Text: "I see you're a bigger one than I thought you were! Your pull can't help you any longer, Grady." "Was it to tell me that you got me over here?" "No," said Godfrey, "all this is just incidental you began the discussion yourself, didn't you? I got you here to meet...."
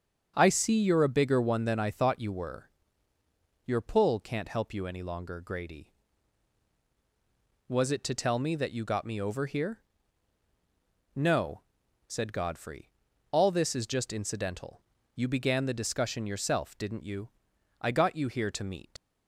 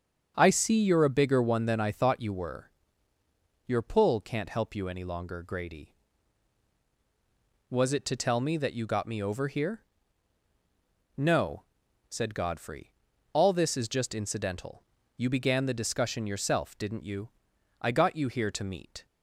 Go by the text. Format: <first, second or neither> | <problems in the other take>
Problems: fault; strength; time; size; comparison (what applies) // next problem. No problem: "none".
second | starts louder than the rest; strong; until 1.3 s; 7.5 dB; strong in the second // pauses between "incidental" and "you"; slight; at 14.8 s; 0.34 s long; slight in the second // leaves "meet" unfinished; at 18.9 s; 85 ms